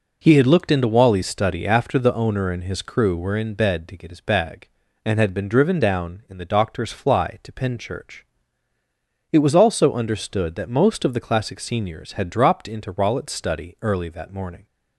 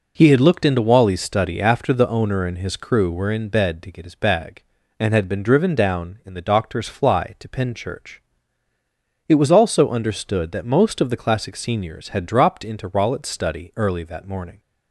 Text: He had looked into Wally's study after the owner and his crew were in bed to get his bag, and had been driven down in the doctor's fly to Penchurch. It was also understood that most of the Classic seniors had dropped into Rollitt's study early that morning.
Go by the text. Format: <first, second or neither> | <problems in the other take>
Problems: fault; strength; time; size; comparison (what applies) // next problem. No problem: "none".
neither | none